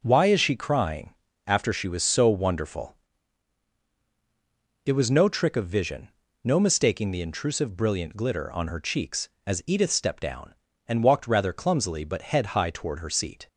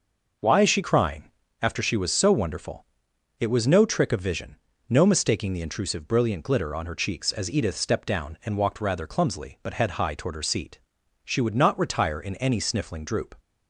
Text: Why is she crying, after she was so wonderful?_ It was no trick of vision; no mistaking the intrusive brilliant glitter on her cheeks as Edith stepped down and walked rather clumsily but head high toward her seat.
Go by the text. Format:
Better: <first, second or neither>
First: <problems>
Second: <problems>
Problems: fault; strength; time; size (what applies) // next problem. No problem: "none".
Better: first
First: none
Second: goes on to say "She would not retire in any sniffling droop"; strong; from 11.2 s on; 2.1 s long